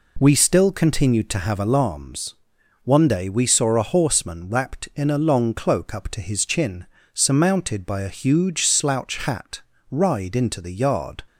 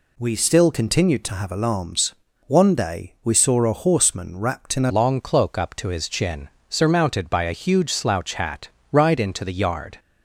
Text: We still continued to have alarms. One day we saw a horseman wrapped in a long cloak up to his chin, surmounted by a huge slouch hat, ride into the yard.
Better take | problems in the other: first | changes voice at "long"; from 4.9 s on; 5.0 s long

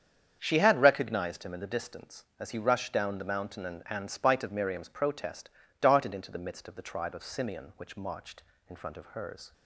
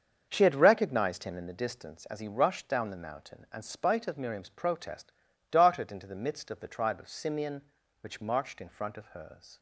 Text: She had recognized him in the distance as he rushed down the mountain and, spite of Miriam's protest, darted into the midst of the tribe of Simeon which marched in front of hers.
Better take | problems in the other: second | starts louder than the rest; strong; until 1.4 s; 7.5 dB; also in the second // says "and" twice; at 3.8 s

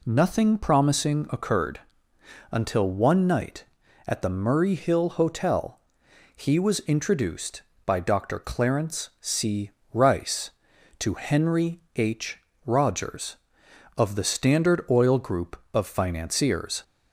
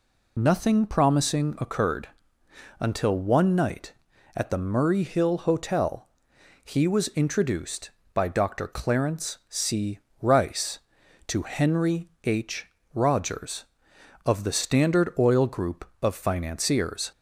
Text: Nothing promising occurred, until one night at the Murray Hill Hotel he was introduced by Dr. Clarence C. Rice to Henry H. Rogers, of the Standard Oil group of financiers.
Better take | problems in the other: first | loses the start of "Nothing"; at 0.3 s; 65 ms // pauses between "Hotel" and "he"; noticeable; at 6.0 s; 0.56 s long; noticeable in the first // pauses between "Henry" and "H"; slight; at 12.0 s; 0.16 s long; slight in the first

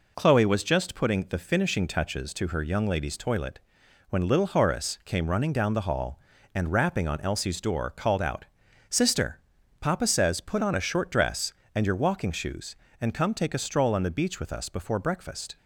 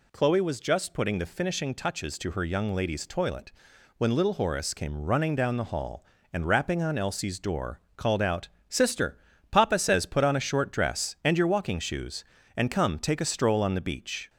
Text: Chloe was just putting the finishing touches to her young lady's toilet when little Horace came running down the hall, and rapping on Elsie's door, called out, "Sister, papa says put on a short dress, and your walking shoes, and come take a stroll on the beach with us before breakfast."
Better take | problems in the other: first | pauses between "toilet" and "when"; noticeable; at 3.5 s; 0.46 s long; noticeable in the first // stops before "with us before breakfast"; at 14.2 s

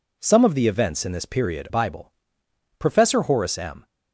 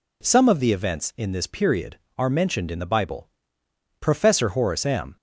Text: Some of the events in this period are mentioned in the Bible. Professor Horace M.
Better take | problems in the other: second | skips "are mentioned in the"; at 1.6 s

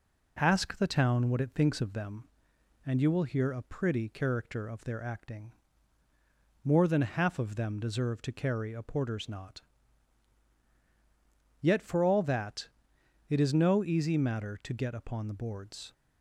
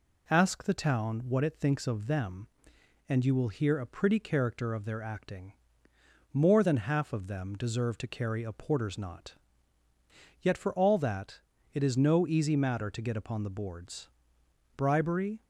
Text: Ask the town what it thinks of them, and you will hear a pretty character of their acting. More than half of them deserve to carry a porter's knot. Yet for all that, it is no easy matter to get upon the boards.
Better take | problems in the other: first | goes on to say "Bribery"; noticeable; from 14.7 s on; 0.66 s long

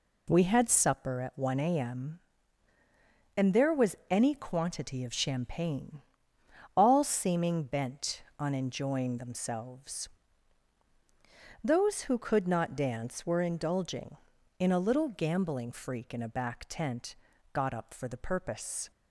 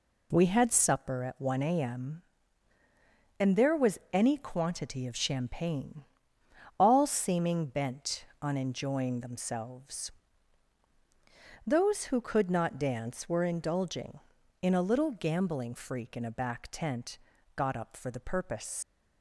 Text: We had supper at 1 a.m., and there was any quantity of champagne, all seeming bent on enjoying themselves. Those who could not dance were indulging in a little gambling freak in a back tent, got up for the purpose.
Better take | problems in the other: first | leaves "purpose" unfinished; at 18.8 s; 105 ms

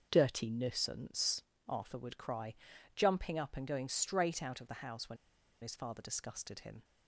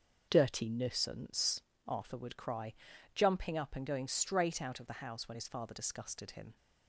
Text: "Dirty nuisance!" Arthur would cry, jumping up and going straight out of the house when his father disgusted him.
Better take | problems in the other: second | starts louder than the rest; until 1.1 s; 6.5 dB; also in the second // pauses between "when" and "his"; noticeable; at 5.1 s; 0.47 s long

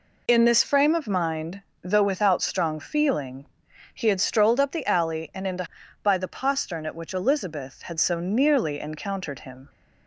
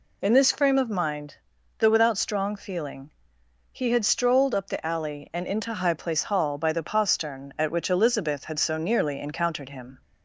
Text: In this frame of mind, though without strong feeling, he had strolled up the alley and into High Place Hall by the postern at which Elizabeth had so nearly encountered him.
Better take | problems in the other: second | skips "High Place Hall"; at 5.8 s

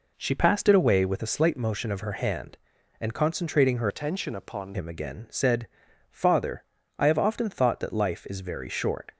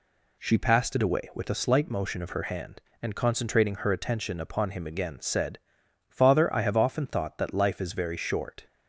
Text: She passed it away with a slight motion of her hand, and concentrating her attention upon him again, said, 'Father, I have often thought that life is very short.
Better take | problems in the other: second | changes voice from "attention" to "upon"; from 3.8 to 4.7 s; 0.9 s long

